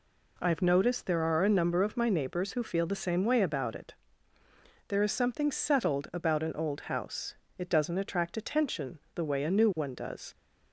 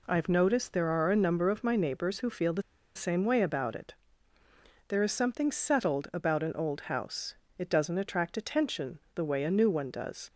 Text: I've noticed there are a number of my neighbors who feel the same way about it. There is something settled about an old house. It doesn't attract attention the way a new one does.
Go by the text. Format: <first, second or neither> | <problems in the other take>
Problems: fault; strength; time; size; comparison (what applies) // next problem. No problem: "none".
first | pauses between "the" and "same"; slight; at 2.6 s; 0.34 s long // pauses between "attention" and "the"; slight; at 8.9 s; 0.16 s long; slight in the first